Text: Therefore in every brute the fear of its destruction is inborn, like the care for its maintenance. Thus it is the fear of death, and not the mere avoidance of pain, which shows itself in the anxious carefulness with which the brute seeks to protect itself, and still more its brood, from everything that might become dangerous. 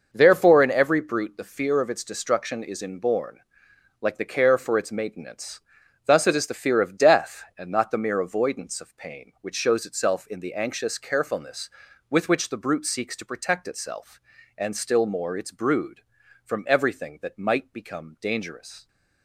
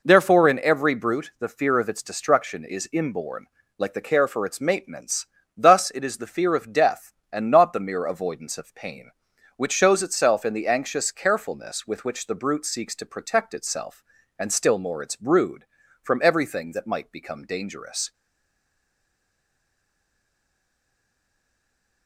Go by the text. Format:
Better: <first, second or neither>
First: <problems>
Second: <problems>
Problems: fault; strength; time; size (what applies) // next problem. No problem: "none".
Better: first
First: none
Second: stays silent after the last word; strong; from 18.1 s on; 3.9 s long